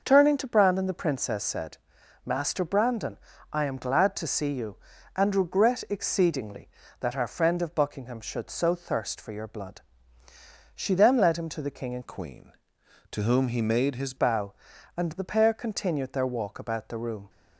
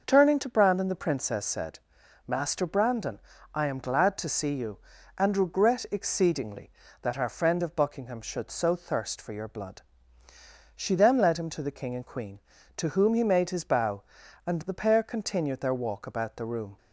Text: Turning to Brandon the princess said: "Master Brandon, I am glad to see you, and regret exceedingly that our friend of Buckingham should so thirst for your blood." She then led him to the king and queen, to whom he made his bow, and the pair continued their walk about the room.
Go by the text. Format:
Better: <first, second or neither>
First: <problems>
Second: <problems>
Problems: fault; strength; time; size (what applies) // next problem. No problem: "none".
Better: second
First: changes voice from "queen" to "his"; from 12.0 to 14.1 s; 2.1 s long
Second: none